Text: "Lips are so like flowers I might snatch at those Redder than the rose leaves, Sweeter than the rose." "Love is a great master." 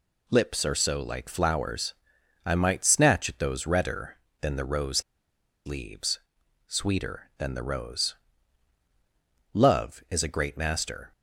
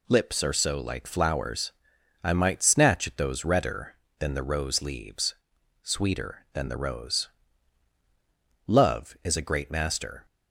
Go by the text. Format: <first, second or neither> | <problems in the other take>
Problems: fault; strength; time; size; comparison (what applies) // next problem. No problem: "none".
second | pauses between "flowers" and "I"; noticeable; at 1.9 s; 0.52 s long; noticeable in the second // pauses between "rose" and "leaves"; noticeable; at 5.0 s; 0.64 s long